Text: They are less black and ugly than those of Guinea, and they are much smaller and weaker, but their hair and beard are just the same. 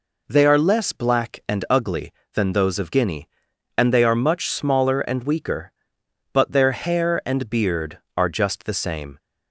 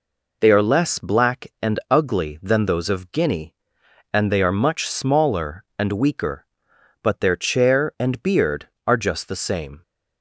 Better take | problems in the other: first | says "chair" for "hair"; at 7.3 s

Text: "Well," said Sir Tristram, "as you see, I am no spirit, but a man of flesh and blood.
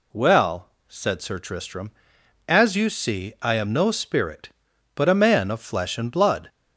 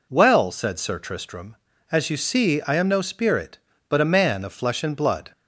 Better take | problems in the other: neither | none

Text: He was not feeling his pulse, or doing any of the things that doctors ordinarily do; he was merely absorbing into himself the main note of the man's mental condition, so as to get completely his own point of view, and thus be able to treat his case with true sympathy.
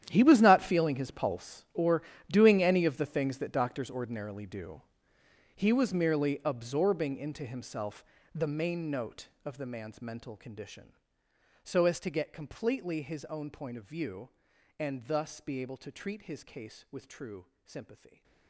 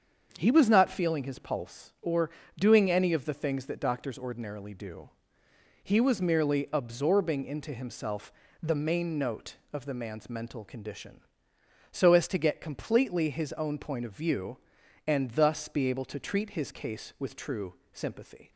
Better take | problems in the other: second | gets quieter; strong; throughout; 16.5 dB // starts louder than the rest; strong; until 1.0 s; 10.5 dB; also in the second // pauses between "or" and "doing"; slight; at 2.0 s; 0.30 s long; slight in the second // pauses between "himself" and "the"; slight; at 8.0 s; 0.32 s long; slight in the second // pauses between "true" and "sympathy"; slight; at 17.4 s; 0.18 s long; slight in the second

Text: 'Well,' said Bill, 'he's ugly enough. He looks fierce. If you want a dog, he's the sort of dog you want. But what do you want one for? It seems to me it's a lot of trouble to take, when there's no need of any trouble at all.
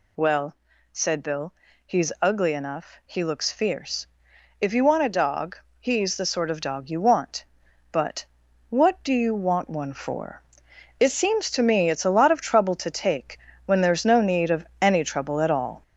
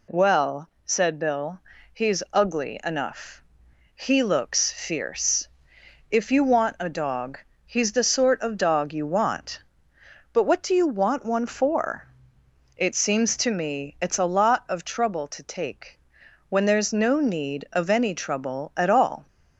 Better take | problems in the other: second | gets louder; noticeable; throughout; 5.5 dB // pauses between "But" and "what"; noticeable; at 8.2 s; 0.46 s long

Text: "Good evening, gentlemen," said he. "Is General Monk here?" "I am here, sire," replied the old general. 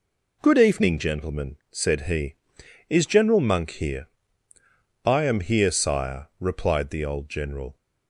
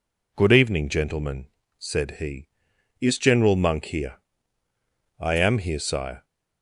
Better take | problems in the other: first | stops before "replied the old general"; at 6.2 s

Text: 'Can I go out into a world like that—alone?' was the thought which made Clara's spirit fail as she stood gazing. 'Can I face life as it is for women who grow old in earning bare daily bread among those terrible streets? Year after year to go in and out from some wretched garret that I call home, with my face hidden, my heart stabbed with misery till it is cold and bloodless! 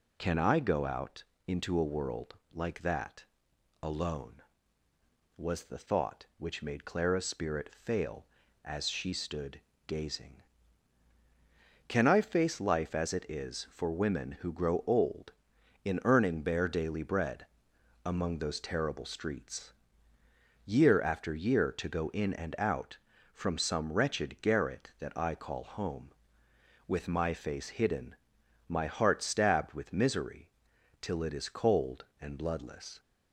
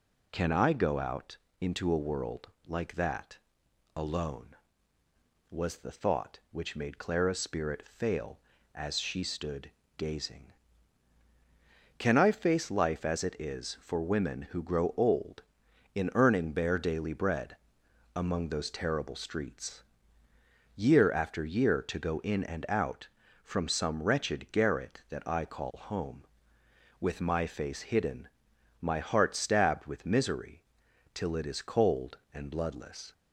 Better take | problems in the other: neither | pauses between "out" and "into"; slight; the same in both // pauses between "world" and "like"; slight; the same in both // pauses between "stood" and "gazing"; slight; the same in both // pauses between "bread" and "among"; noticeable; the same in both // pauses between "misery" and "till"; noticeable; the same in both

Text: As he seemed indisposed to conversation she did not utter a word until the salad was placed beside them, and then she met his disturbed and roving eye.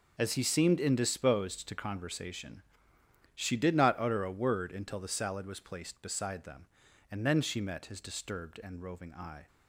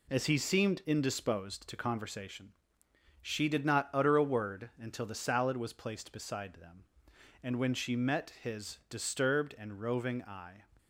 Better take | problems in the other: first | pauses between "conversation" and "she"; noticeable; at 2.5 s; 0.68 s long; noticeable in the first // says "when" for "then"; at 7.5 s

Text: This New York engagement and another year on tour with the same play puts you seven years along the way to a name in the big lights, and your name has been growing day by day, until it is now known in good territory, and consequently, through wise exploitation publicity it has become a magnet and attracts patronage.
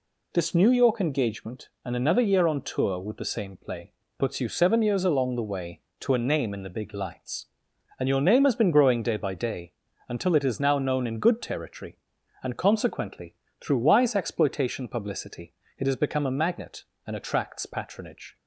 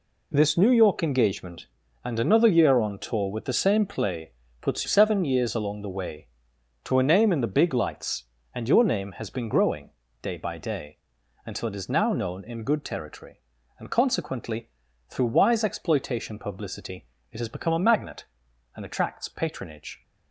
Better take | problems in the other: first | pauses between "play" and "puts"; slight; at 4.3 s; 0.32 s long; slight in the first // skips "you"; at 4.8 s // pauses between "growing" and "day"; slight; at 9.9 s; 0.32 s long // pauses between "publicity" and "it"; slight; at 17.0 s; 0.28 s long; slight in the first

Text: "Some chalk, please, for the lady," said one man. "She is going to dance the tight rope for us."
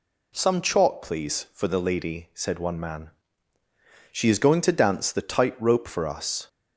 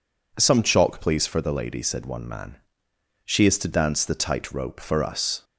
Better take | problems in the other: first | skips "going"; at 3.5 s

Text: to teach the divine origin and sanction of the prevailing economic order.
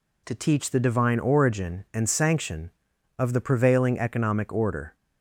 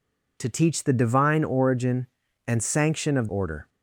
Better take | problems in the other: first | skips "the prevailing economic"; at 3.2 s

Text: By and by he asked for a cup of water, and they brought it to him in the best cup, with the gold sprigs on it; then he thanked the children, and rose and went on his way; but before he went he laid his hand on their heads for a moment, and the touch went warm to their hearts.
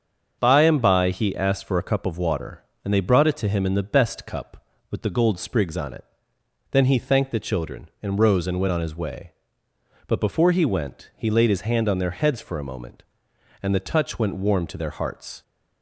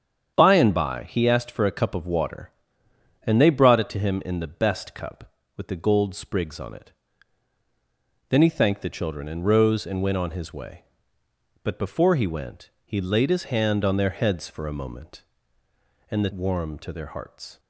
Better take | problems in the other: first | starts louder than the rest; strong; until 1.3 s; 8 dB; strong in the first // pauses between "went" and "he"; slight; at 12.6 s; 0.16 s long // skips "touch went"; at 16.3 s

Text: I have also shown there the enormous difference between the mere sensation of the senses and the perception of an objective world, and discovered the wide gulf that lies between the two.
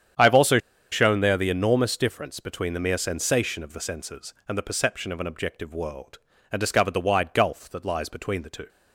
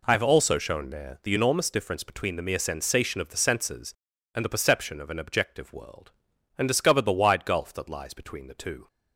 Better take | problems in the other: second | starts louder than the rest; strong; until 1.5 s; 8.5 dB // pauses between "also" and "shown"; slight; at 0.5 s; 0.32 s long

